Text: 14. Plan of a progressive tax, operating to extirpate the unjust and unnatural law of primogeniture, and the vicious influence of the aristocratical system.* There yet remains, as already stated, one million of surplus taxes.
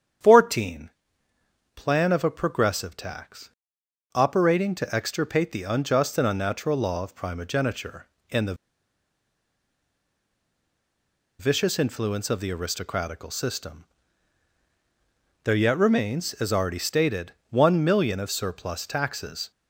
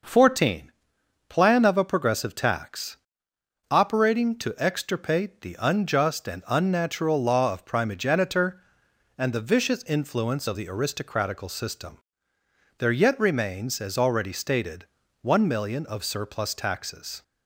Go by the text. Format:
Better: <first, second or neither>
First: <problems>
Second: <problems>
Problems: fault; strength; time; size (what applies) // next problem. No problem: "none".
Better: second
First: starts louder than the rest; strong; until 2.0 s; 8.5 dB // pauses between "the" and "vicious"; strong; at 8.5 s; 2.8 s long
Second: none